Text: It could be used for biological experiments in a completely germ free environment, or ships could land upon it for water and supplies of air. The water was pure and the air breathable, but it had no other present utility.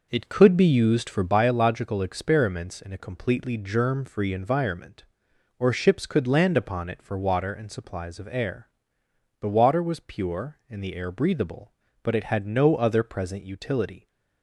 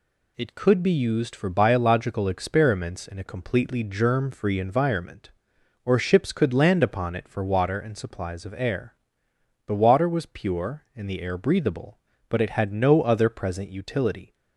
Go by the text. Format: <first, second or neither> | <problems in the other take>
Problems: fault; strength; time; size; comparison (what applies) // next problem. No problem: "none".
second | starts louder than the rest; noticeable; until 1.3 s; 5 dB